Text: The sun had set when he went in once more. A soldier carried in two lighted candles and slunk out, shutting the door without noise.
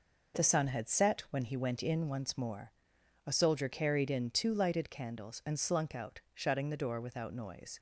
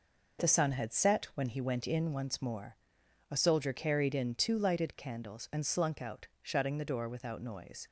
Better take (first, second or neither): neither